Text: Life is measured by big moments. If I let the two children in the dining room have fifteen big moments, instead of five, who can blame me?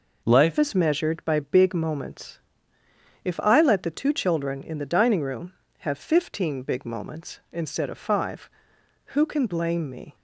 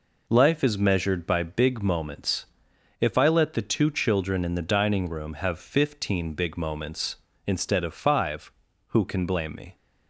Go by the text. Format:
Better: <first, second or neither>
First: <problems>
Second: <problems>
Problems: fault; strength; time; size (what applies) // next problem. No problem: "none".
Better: second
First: changes voice at "is"; from 0.5 s on; 9.6 s long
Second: none